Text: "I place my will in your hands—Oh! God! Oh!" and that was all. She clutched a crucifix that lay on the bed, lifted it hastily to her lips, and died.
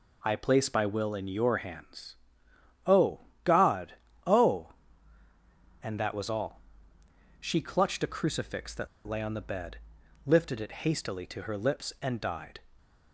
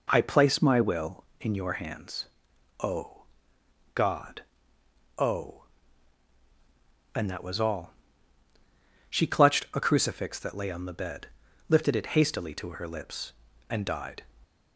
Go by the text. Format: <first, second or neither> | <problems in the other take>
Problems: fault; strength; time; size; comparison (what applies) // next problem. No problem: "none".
second | pauses between "that" and "lay"; slight; at 8.8 s; 0.19 s long